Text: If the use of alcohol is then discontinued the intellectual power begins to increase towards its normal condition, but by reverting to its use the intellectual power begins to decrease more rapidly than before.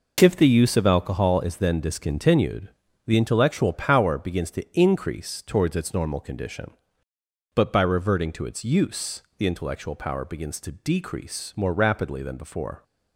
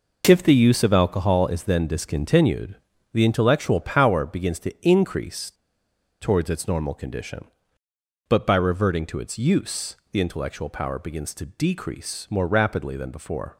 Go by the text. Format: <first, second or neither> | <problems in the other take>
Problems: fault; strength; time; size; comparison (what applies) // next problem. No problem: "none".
first | pauses between "discontinued" and "the"; at 2.7 s; 0.38 s long; also in the first // pauses between "increase" and "towards"; noticeable; at 5.5 s; 0.69 s long // pauses between "use" and "the"; slight; at 9.9 s; 0.16 s long; slight in the first